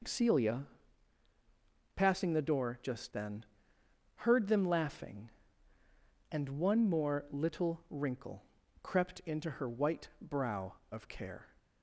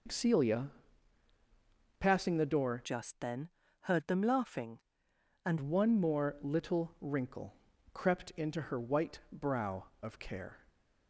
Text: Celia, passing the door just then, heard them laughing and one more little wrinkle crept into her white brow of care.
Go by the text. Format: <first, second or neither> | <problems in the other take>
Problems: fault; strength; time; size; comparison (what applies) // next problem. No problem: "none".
first | changes voice from "just" to "and"; from 2.8 to 5.5 s; 2.7 s long // pauses between "wrinkle" and "crept"; at 7.5 s; 0.38 s long; also in the first